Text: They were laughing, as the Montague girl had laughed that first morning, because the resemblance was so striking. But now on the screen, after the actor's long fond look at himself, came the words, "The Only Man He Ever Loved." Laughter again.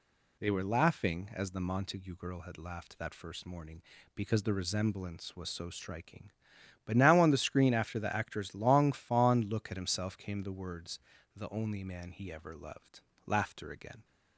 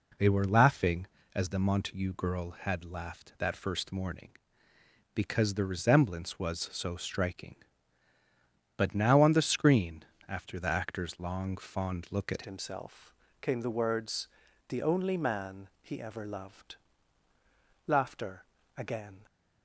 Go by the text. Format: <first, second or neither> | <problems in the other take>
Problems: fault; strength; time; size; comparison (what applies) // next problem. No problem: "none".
first | changes voice at "himself"; from 12.4 s on; 6.8 s long // pauses between "Laughter" and "again"; slight; at 18.4 s; 0.34 s long